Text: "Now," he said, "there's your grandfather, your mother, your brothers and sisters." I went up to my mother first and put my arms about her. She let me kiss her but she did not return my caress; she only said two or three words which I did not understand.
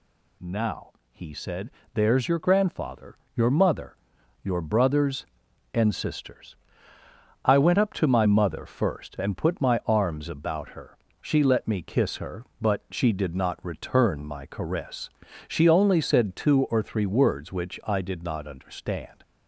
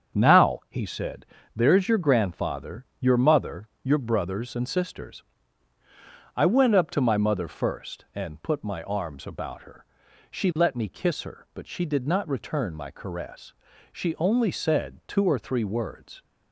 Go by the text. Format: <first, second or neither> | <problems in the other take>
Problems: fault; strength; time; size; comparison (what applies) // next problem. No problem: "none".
first | starts louder than the rest; strong; until 1.2 s; 7.5 dB // stops before "which I did not understand"; at 16.2 s